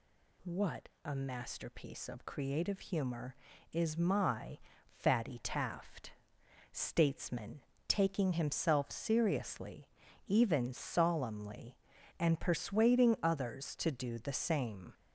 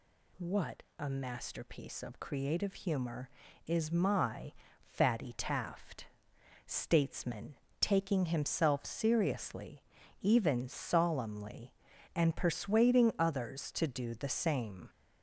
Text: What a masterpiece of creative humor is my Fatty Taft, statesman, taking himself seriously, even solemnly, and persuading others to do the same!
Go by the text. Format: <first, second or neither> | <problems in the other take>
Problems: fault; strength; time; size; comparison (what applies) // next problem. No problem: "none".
neither | pauses between "What" and "a"; slight; the same in both // pauses between "my" and "Fatty"; slight; the same in both